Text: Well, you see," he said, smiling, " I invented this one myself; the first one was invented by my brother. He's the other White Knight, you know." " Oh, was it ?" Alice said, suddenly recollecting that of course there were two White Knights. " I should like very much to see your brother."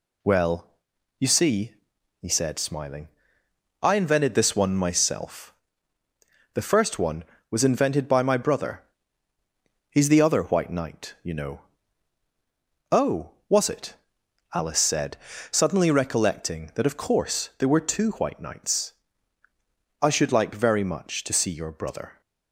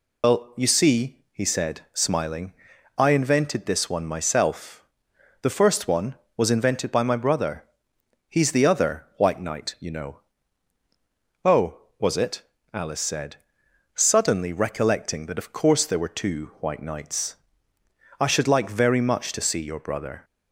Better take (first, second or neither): first